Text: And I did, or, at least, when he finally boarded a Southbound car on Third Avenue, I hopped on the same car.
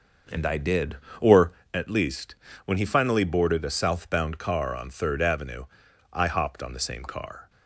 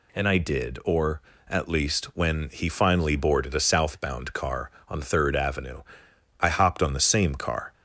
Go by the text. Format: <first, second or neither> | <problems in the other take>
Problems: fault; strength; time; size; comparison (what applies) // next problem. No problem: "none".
second | starts louder than the rest; noticeable; until 1.7 s; 6 dB